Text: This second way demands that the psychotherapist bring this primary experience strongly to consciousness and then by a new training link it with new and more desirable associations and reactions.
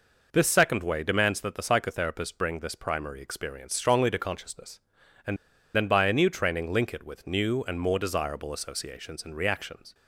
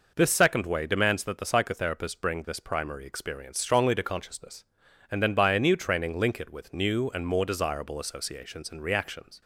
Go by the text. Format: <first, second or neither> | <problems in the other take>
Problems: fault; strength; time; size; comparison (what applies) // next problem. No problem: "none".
second | pauses between "and" and "then"; at 5.3 s; 0.38 s long